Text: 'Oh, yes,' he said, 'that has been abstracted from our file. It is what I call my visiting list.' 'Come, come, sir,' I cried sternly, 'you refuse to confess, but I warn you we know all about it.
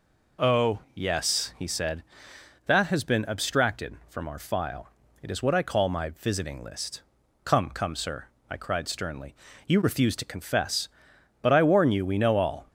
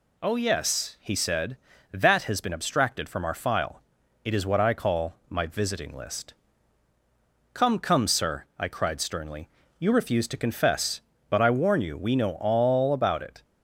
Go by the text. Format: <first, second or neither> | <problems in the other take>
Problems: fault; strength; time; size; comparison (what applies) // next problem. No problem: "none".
second | stops before "about it"; at 12.6 s